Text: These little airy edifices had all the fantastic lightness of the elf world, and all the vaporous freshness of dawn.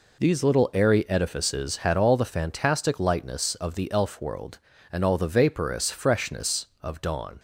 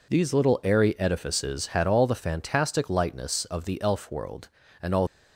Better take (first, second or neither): first